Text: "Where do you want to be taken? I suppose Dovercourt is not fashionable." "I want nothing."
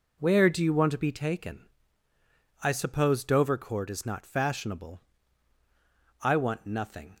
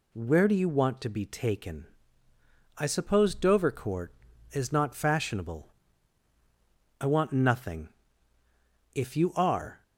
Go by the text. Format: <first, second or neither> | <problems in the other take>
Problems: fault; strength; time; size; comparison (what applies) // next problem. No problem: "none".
first | goes on to say "If you are"; noticeable; from 8.9 s on; 0.90 s long